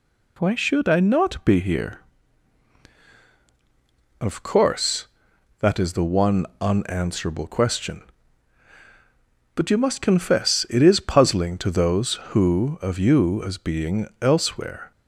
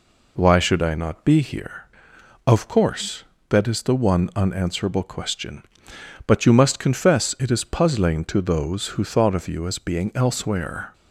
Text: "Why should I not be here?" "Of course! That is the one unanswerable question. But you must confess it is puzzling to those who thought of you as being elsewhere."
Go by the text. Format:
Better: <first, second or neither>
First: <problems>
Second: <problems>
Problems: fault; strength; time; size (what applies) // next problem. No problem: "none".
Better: second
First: pauses between "one" and "unanswerable"; slight; at 6.4 s; 0.16 s long // skips "thought"; at 12.8 s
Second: none